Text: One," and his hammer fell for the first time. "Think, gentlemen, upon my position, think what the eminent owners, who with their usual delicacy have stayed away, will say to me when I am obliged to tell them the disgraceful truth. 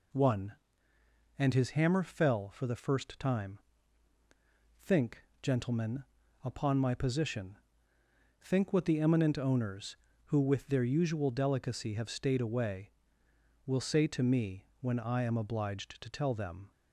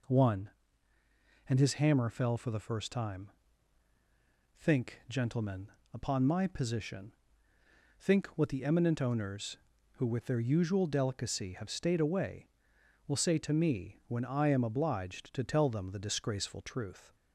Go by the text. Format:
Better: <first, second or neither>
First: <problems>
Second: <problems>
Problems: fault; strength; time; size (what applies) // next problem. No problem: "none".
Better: second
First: pauses between "me" and "when"; slight; at 14.6 s; 0.16 s long // stops before "the disgraceful truth"; at 16.7 s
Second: none